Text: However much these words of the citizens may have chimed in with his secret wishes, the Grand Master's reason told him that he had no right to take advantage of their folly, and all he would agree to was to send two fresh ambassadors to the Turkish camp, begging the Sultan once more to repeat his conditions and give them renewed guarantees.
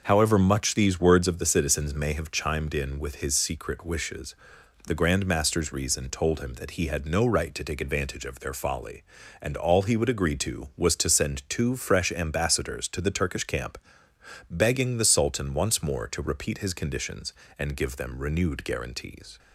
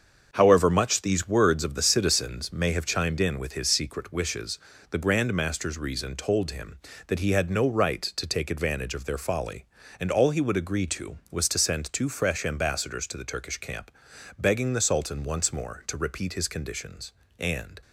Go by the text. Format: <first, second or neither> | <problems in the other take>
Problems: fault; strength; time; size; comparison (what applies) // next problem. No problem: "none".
first | starts louder than the rest; until 1.3 s; 6.5 dB // stops before "give them renewed guarantees"; at 17.8 s